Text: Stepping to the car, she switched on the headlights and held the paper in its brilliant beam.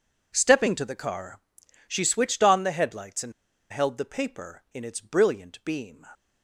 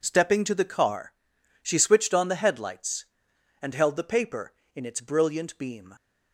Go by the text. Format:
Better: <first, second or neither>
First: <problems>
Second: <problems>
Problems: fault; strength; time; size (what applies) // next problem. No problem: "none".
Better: second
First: pauses between "and" and "held"; at 3.3 s; 0.39 s long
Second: none